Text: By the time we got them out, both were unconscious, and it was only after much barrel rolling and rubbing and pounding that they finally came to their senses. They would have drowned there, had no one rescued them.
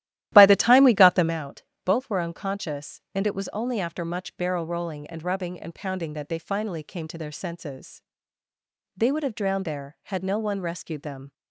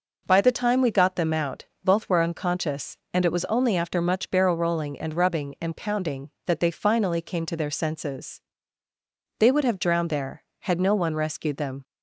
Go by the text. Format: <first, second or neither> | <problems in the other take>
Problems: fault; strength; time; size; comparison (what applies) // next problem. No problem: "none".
second | starts louder than the rest; strong; until 1.4 s; 13.5 dB